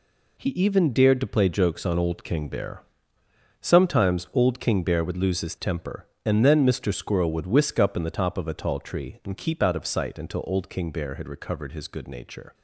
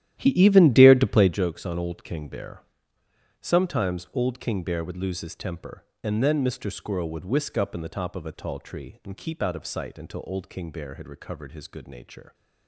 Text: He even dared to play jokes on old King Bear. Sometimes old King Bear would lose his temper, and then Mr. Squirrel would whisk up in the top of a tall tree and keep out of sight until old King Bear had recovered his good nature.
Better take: first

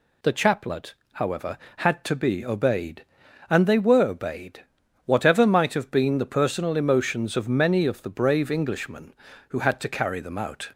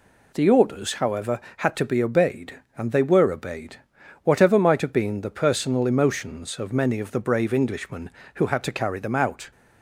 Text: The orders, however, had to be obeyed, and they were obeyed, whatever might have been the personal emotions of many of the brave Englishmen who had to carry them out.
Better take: second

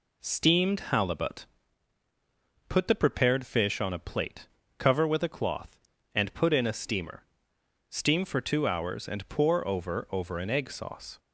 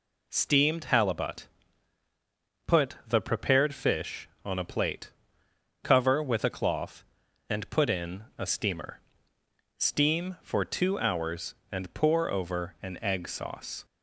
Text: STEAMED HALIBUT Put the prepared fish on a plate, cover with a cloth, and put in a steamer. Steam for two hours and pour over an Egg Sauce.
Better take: second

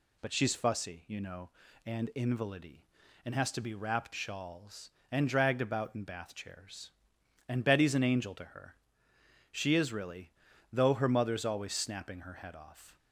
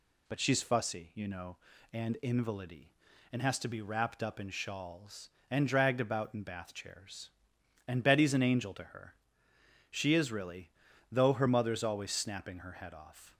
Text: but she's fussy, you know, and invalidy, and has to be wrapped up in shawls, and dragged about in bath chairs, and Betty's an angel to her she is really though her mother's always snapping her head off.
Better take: second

